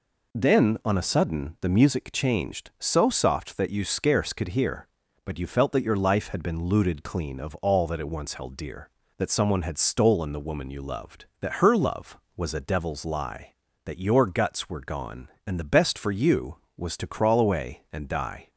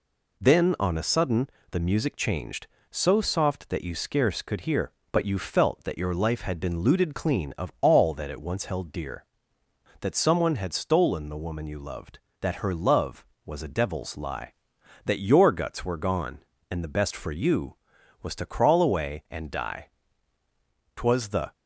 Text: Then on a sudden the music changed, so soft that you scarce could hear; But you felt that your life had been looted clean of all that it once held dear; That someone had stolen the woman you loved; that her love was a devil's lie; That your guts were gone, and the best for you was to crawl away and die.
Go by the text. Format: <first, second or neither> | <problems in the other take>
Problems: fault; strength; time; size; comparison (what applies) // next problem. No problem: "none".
first | pauses between "sudden" and "the"; slight; at 1.4 s; 0.22 s long // goes on to say "Twas the"; from 20.9 s on; 0.58 s long